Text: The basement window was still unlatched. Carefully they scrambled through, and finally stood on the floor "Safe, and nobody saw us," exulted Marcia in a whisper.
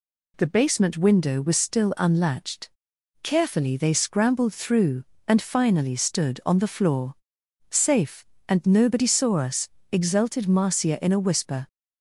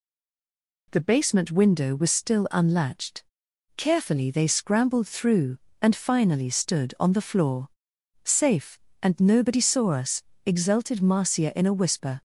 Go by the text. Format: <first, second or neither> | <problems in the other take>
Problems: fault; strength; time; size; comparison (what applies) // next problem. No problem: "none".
first | stays silent before the first word; slight; until 0.9 s; 0.9 s long // pauses between "floor" and "Safe"; noticeable; at 7.6 s; 0.56 s long; noticeable in the first